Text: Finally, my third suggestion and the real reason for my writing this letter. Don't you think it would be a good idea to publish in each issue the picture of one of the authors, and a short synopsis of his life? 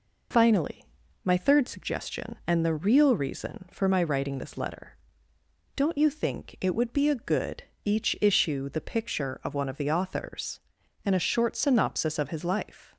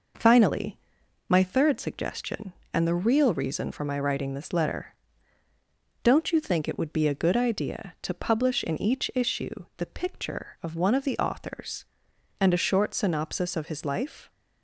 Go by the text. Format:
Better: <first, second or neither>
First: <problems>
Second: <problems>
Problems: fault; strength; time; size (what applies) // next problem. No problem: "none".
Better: second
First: skips "idea to publish in"; at 7.7 s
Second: none